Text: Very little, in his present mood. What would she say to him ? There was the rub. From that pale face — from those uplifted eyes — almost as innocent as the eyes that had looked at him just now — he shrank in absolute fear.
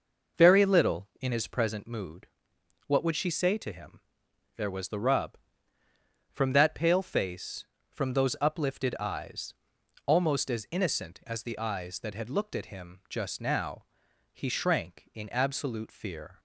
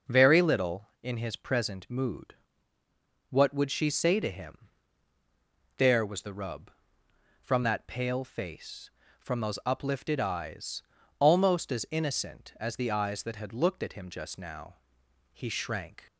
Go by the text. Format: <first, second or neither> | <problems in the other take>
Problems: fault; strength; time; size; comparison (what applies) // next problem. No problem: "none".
first | stops before "in absolute fear"; at 16.0 s